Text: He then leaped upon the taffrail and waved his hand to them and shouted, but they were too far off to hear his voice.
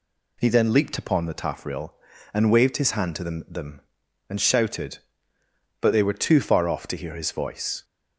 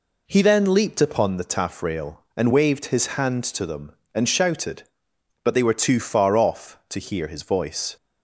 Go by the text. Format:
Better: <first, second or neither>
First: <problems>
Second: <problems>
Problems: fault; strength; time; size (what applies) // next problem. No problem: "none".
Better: second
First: says "them" twice; at 3.4 s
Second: none